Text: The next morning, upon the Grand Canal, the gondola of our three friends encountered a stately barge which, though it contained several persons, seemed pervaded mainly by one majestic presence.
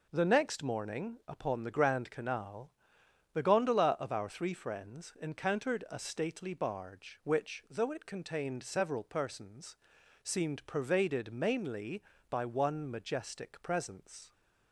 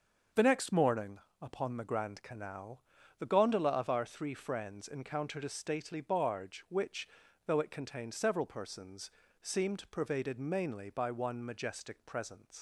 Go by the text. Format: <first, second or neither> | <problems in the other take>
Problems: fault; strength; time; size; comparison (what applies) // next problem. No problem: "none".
first | starts louder than the rest; until 1.5 s; 6.5 dB // leaves "presence" unfinished; at 12.5 s; 105 ms